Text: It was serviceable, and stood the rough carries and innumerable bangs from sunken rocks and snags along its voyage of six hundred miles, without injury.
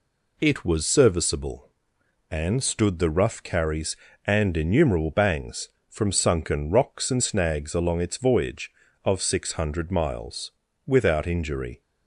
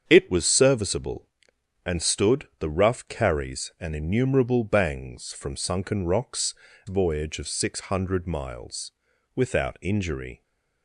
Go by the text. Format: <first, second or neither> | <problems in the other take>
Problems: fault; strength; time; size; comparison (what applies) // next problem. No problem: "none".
first | starts louder than the rest; strong; until 1.0 s; 7.5 dB // skips "and snags along its"; at 6.7 s